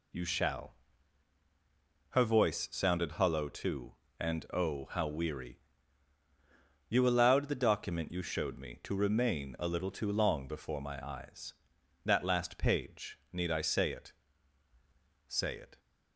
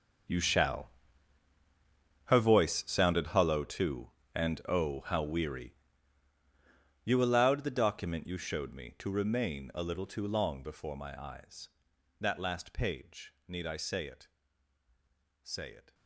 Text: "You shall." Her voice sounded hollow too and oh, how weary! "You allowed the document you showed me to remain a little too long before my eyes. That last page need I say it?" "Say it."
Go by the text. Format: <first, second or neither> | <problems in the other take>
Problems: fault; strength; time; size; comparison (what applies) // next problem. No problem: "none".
first | gets quieter; strong; throughout; 16.5 dB